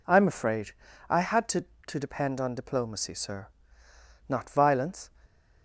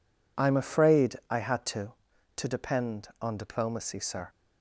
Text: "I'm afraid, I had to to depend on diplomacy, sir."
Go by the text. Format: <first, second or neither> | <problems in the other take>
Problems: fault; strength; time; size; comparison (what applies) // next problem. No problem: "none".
second | goes on to say "Not violence"; noticeable; from 4.2 s on; 0.82 s long